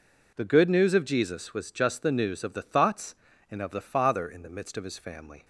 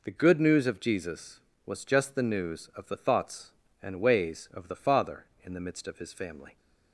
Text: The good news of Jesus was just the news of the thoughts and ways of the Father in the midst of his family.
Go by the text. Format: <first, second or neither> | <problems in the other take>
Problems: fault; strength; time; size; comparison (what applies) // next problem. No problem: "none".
second | skips "ways"; at 3.6 s